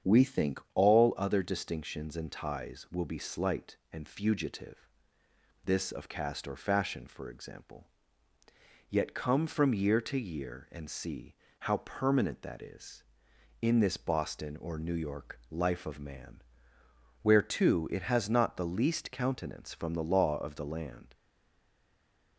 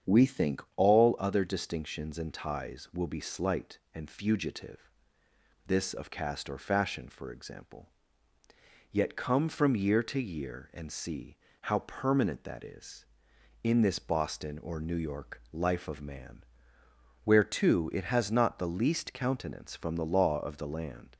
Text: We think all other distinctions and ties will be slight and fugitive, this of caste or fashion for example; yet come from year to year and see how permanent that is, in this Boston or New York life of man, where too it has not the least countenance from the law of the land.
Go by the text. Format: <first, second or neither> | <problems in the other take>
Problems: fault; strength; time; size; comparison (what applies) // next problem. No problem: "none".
second | starts louder than the rest; strong; until 1.2 s; 8 dB; strong in the second // pauses between "see" and "how"; slight; at 11.3 s; 0.24 s long; slight in the second // stays silent after the last word; noticeable; from 21.1 s on; 1.2 s long